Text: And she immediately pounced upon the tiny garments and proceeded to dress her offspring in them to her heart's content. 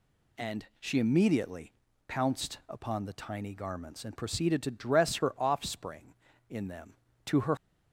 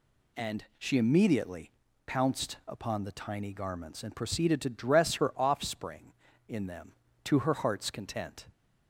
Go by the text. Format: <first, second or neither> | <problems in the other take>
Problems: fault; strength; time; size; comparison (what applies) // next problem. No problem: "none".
second | pauses between "immediately" and "pounced"; slight; at 1.7 s; 0.36 s long; slight in the second // stops before "heart's content"; at 7.5 s